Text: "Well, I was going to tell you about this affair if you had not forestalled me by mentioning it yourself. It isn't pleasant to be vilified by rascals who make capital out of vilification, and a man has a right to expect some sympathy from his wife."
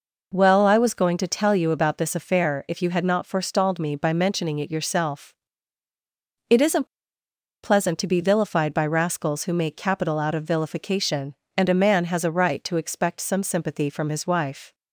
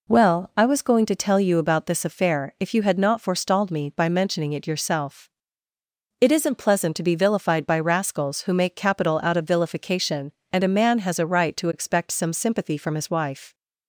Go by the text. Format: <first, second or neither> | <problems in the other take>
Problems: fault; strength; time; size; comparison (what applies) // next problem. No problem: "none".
second | pauses between "isn't" and "pleasant"; noticeable; at 6.8 s; 0.76 s long